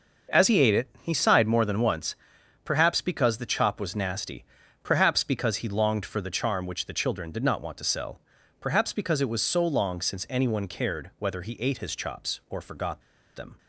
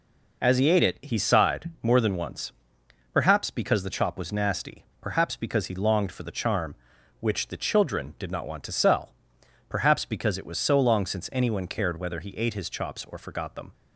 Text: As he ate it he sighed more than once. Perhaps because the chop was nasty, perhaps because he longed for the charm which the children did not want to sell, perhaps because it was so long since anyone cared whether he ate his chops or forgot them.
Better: second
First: starts louder than the rest; noticeable; until 1.4 s; 6 dB // pauses between "forgot" and "them"; slight; at 13.0 s; 0.34 s long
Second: none

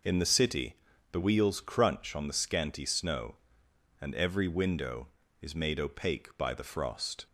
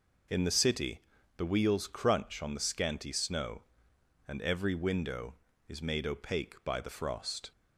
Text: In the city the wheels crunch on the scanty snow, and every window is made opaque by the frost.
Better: neither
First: pauses between "city" and "the"; slight; at 0.7 s; 0.36 s long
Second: pauses between "city" and "the"; slight; at 1.0 s; 0.36 s long

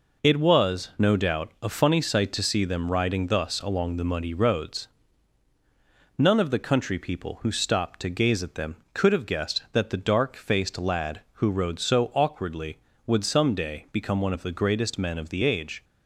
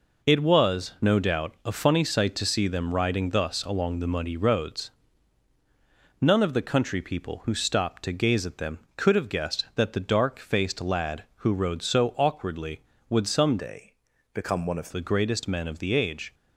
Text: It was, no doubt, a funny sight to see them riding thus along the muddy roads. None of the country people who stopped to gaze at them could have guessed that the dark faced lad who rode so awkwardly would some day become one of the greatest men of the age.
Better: first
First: none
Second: changes voice from "day" to "of"; from 13.5 to 14.8 s; 1.3 s long // pauses between "day" and "become"; at 13.9 s; 0.38 s long

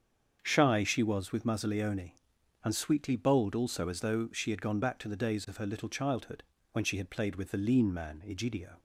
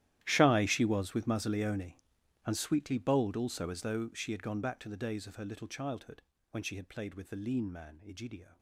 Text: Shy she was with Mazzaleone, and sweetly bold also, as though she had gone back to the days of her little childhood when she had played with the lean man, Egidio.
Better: first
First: starts louder than the rest; strong; until 1.4 s; 7 dB // pauses between "childhood" and "when"; slight; at 6.4 s; 0.28 s long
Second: gets quieter; strong; throughout; 19.5 dB // starts louder than the rest; strong; until 1.2 s; 13 dB // pauses between "childhood" and "when"; slight; at 6.2 s; 0.28 s long

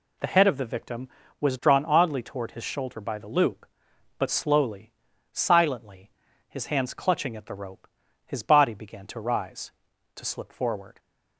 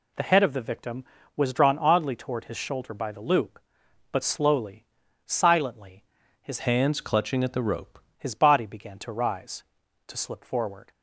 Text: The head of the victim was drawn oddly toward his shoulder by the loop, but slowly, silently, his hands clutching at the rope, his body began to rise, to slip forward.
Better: first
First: none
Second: changes voice from "hands" to "rope"; from 6.5 to 7.9 s; 1.4 s long

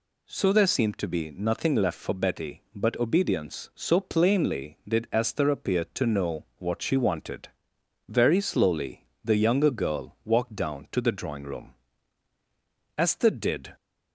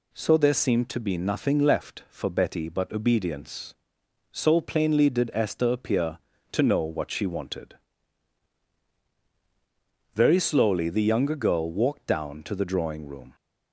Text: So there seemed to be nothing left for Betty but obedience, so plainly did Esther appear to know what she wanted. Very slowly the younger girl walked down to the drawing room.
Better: second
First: pauses between "slowly" and "the"; slight; at 9.0 s; 0.18 s long // goes on to say "Esther did"; noticeable; from 12.9 s on; 0.78 s long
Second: none

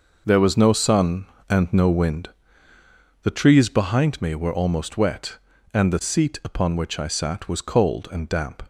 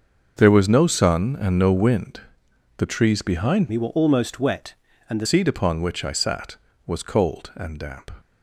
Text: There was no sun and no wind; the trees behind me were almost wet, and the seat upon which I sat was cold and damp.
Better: first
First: none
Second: starts louder than the rest; until 1.4 s; 6 dB // changes voice from "me" to "the"; from 3.6 to 5.2 s; 1.6 s long

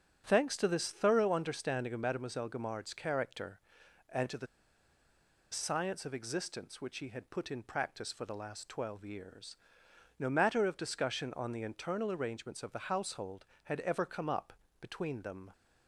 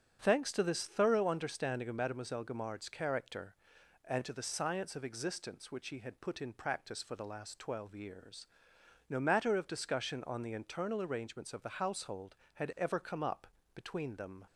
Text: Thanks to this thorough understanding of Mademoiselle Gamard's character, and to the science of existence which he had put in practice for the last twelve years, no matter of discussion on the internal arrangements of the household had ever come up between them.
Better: second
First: starts louder than the rest; strong; until 1.2 s; 7 dB // pauses between "the" and "science"; at 4.4 s; 1.0 s long // pauses between "up" and "between"; slight; at 14.5 s; 0.26 s long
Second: starts louder than the rest; strong; until 1.2 s; 7.5 dB // pauses between "up" and "between"; slight; at 13.4 s; 0.26 s long

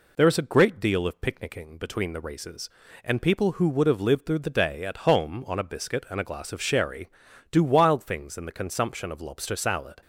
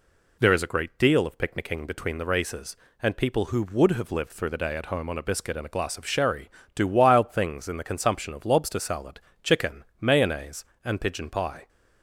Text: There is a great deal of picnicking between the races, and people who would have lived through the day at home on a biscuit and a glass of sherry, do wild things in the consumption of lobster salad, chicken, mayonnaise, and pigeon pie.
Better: second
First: stops before "chicken mayonnaise and pigeon pie"; at 10.0 s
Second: none

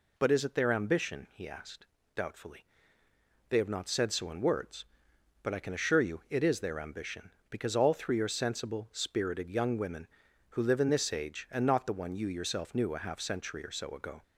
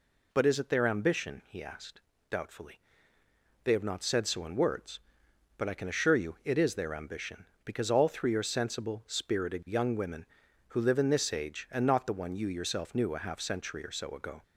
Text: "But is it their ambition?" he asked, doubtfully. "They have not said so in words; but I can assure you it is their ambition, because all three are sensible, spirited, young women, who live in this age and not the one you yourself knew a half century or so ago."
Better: neither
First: none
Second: none

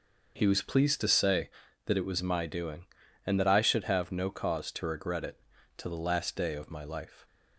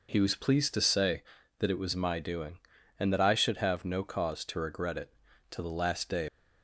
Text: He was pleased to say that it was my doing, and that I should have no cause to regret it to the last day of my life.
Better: first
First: none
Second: stops before "of my life"; at 6.2 s

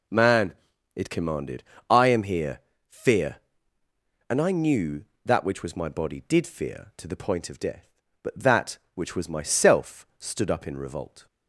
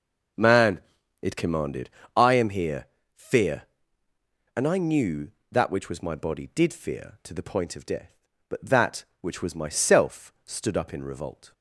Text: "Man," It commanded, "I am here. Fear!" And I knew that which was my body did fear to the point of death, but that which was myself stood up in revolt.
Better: first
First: none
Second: starts louder than the rest; noticeable; until 2.2 s; 5.5 dB

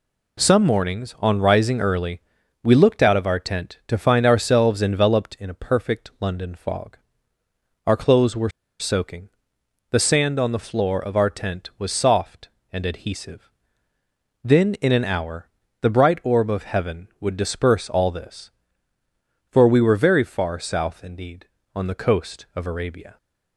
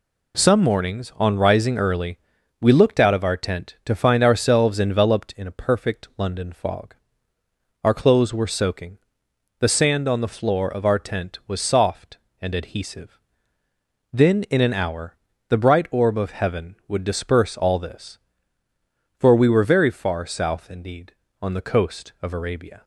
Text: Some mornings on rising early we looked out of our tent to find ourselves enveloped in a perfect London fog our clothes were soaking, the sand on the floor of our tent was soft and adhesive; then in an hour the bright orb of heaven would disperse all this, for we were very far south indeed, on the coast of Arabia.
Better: second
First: pauses between "early" and "we"; at 2.2 s; 0.42 s long // pauses between "fog" and "our"; noticeable; at 6.9 s; 0.88 s long // pauses between "were" and "soaking"; slight; at 8.5 s; 0.29 s long // pauses between "hour" and "the"; slight; at 15.4 s; 0.36 s long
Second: pauses between "early" and "we"; at 2.1 s; 0.42 s long // pauses between "fog" and "our"; noticeable; at 6.9 s; 0.88 s long // pauses between "hour" and "the"; slight; at 15.1 s; 0.36 s long

